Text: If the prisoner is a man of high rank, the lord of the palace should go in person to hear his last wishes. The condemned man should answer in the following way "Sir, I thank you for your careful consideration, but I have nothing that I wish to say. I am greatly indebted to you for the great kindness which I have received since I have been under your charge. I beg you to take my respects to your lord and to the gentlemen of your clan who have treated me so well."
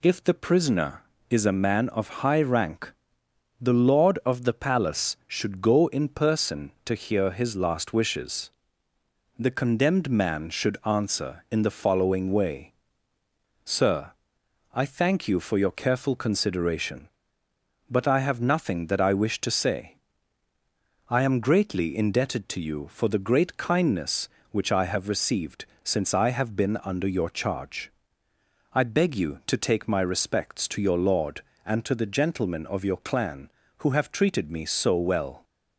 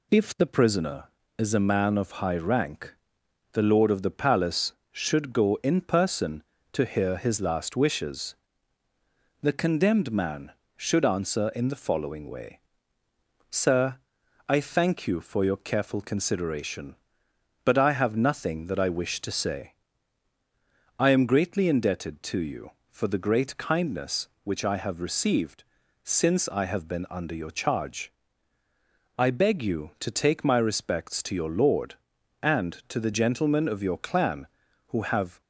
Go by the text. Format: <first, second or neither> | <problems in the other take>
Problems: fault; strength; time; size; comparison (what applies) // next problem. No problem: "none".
first | pauses between "way" and "Sir"; noticeable; at 12.5 s; 0.92 s long; noticeable in the first // pauses between "received" and "since"; at 25.6 s; 0.38 s long; slight in the first // stops before "treated me so well"; at 35.4 s